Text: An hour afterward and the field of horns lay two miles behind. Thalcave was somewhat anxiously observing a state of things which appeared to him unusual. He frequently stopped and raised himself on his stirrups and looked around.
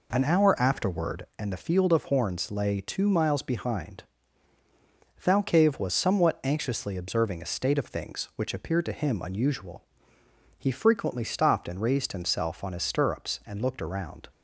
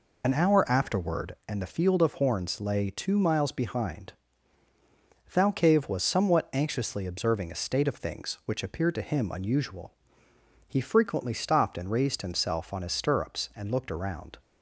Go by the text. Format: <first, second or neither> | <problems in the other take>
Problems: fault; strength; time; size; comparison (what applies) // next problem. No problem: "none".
first | loses the start of "An"; at 0.2 s; 50 ms